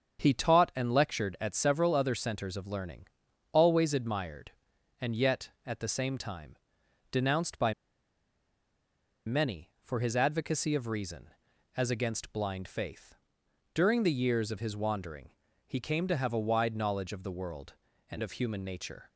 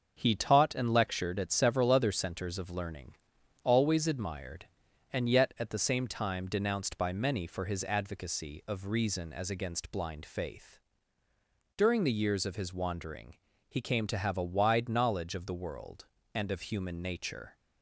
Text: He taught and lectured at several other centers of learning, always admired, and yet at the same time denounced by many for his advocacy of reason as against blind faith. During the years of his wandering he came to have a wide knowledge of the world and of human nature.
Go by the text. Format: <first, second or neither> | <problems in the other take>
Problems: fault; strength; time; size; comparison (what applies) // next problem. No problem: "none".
second | starts louder than the rest; until 1.2 s; 7 dB; also in the second // pauses between "time" and "denounced"; noticeable; at 6.5 s; 0.52 s long // pauses between "by" and "many"; strong; at 7.7 s; 1.5 s long // pauses between "wandering" and "he"; slight; at 15.2 s; 0.36 s long; slight in the second